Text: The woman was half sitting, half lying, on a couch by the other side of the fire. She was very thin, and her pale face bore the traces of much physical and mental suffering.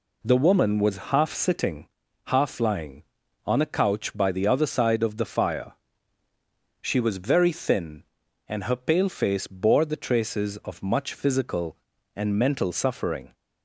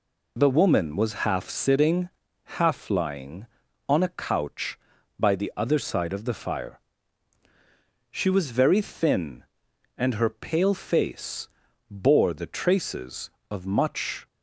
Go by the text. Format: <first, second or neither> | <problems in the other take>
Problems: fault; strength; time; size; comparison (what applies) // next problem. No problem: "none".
first | pauses between "face" and "bore"; at 11.4 s; 0.42 s long // stops before "physical and mental suffering"; at 14.2 s